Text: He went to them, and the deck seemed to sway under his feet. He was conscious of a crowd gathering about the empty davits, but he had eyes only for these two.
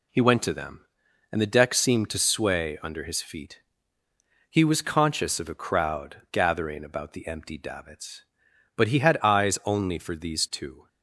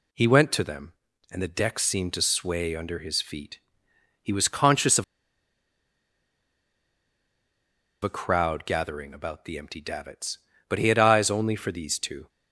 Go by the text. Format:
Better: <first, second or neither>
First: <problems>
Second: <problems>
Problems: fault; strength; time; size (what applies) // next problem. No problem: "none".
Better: first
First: none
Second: pauses between "of" and "a"; strong; at 5.0 s; 3.0 s long